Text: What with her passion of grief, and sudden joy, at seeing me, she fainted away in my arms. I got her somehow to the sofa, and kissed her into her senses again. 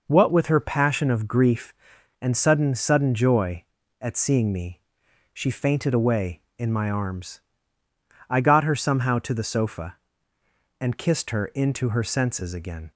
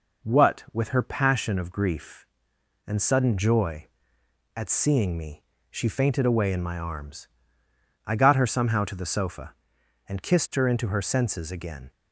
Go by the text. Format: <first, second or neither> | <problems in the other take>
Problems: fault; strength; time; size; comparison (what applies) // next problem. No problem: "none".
second | says "sudden" twice; at 2.7 s